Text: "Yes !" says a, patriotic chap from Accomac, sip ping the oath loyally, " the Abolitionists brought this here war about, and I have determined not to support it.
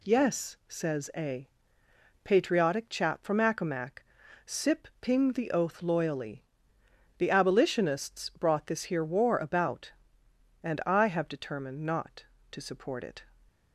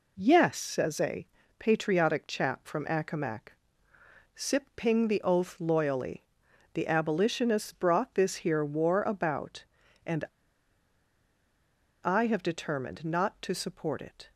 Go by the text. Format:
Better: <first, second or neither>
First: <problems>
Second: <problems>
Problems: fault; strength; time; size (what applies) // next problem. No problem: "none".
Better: first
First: none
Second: pauses between "and" and "I"; strong; at 10.2 s; 1.7 s long